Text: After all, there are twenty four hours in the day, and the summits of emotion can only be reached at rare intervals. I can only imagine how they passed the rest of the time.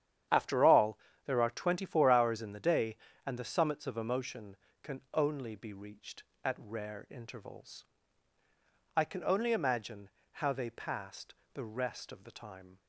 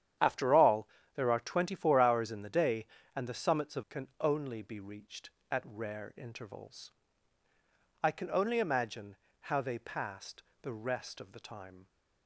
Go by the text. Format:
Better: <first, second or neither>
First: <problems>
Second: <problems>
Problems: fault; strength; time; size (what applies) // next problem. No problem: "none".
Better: first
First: starts louder than the rest; strong; until 1.5 s; 10 dB // pauses between "imagine" and "how"; slight; at 10.0 s; 0.22 s long // pauses between "passed" and "the"; slight; at 11.3 s; 0.18 s long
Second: starts louder than the rest; strong; until 1.4 s; 10 dB // skips "emotion"; at 3.8 s // pauses between "imagine" and "how"; slight; at 9.1 s; 0.24 s long // pauses between "passed" and "the"; slight; at 10.4 s; 0.18 s long